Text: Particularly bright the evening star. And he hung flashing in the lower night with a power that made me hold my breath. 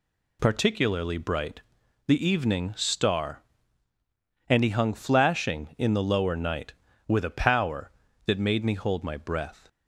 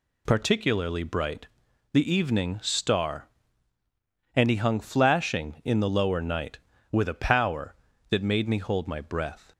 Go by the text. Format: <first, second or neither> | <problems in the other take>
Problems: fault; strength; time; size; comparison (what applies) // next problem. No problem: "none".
neither | pauses between "bright" and "the"; noticeable; the same in both